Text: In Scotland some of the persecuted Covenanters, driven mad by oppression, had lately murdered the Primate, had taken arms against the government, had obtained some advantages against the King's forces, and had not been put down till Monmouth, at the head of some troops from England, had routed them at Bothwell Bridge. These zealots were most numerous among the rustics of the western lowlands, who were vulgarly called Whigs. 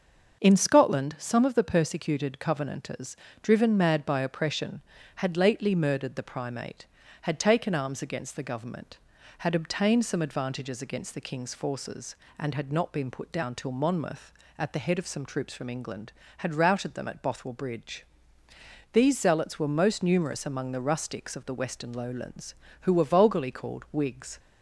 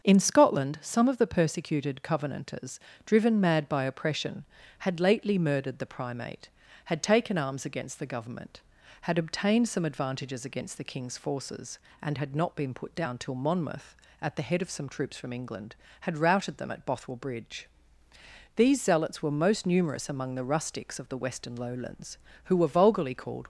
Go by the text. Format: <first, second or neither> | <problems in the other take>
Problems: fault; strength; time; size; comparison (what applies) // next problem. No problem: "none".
first | starts louder than the rest; until 1.0 s; 6.5 dB; also in the first // stops before "Whigs"; at 23.4 s